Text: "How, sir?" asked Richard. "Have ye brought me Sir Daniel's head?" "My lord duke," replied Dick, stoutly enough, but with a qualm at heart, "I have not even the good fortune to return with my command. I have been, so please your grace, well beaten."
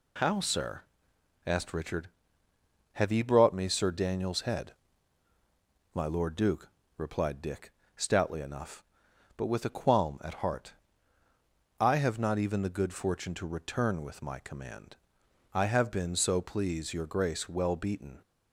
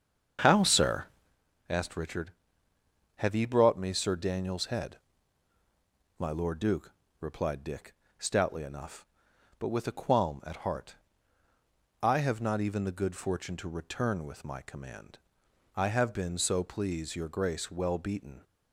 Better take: first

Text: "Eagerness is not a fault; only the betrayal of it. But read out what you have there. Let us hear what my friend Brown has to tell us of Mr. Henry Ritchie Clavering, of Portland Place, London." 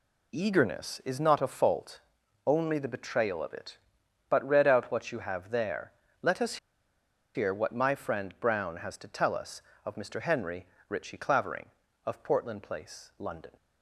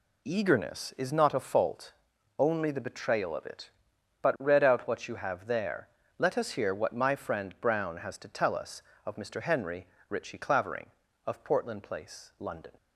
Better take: second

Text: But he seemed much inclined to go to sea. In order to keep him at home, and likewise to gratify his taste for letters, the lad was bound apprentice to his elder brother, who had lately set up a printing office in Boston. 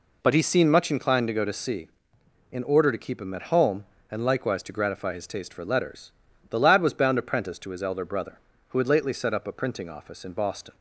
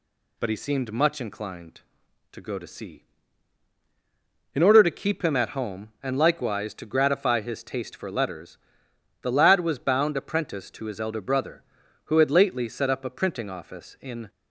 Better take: first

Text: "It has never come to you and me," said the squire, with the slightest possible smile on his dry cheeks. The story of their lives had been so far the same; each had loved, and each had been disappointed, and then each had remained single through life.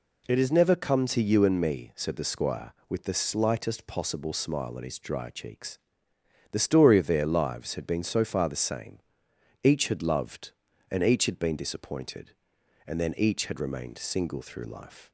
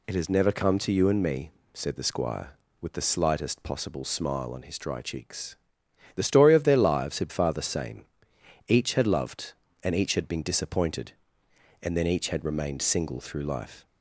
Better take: first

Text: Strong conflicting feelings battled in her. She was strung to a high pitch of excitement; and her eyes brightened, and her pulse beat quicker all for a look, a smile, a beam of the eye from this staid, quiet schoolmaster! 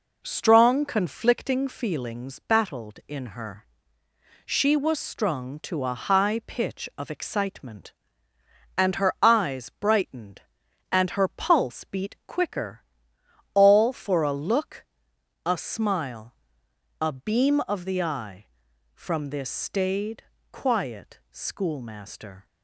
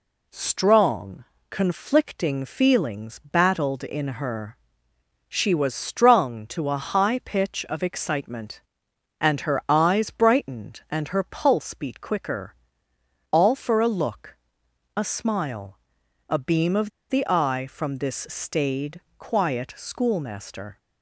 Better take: first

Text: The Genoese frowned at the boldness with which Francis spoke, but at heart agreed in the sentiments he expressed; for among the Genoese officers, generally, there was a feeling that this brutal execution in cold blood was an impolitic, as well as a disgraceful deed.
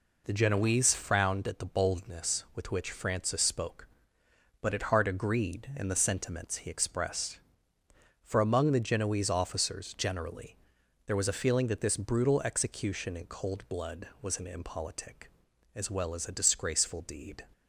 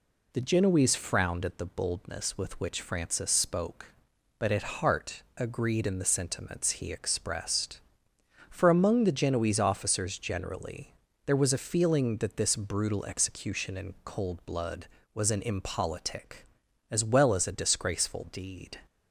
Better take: neither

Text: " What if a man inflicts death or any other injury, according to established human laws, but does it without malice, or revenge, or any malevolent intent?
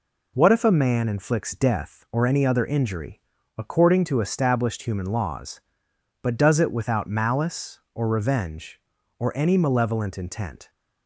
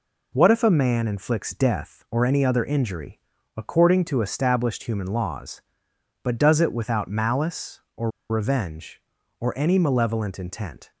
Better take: first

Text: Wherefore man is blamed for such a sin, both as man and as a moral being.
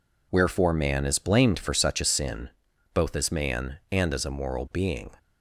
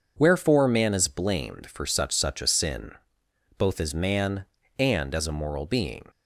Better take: first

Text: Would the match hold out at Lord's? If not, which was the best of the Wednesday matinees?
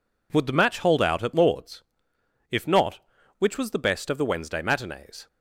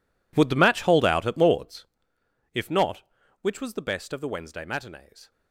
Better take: first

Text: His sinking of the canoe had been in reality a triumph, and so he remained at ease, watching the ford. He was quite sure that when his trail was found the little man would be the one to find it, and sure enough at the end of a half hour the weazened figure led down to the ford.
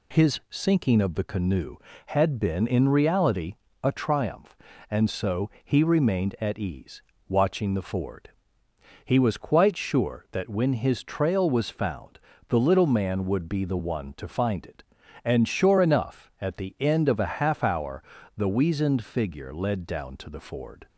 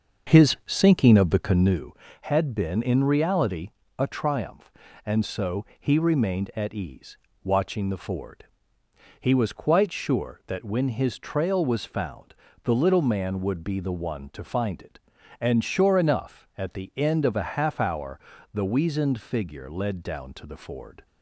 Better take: first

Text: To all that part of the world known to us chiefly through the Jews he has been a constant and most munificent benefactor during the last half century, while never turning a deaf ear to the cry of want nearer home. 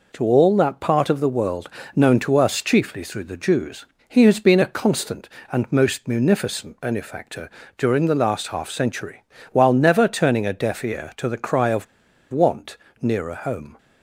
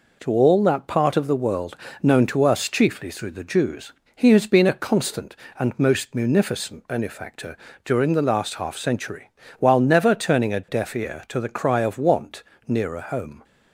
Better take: second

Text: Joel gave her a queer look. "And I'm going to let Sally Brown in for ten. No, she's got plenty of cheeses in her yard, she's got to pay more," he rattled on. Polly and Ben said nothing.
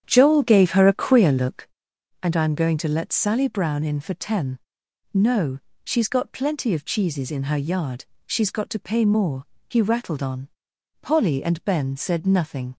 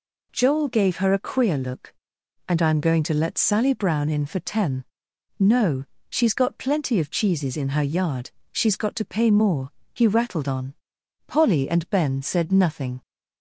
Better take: second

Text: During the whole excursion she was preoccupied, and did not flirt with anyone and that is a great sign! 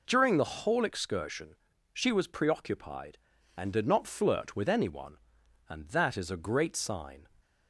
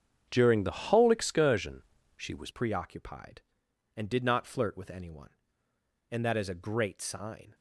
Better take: first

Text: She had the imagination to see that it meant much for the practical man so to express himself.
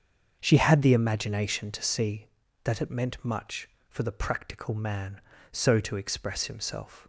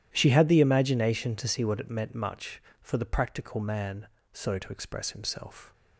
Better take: first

